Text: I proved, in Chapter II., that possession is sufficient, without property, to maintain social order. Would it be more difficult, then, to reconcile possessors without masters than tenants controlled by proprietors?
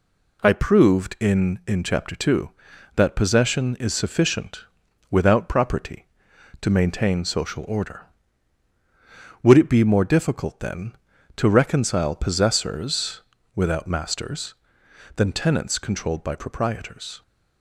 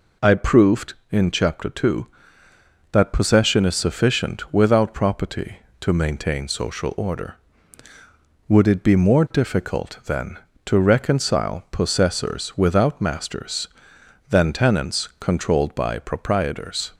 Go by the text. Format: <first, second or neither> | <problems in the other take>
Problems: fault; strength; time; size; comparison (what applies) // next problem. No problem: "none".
second | says "in" twice; at 1.6 s // pauses between "possessors" and "without"; slight; at 13.2 s; 0.34 s long